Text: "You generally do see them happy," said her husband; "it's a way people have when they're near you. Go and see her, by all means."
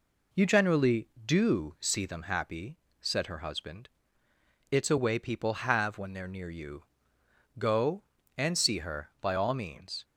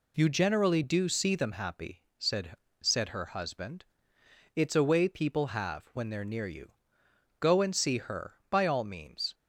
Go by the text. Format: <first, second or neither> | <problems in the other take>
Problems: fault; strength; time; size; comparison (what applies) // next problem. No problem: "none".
first | says "said" twice; at 2.8 s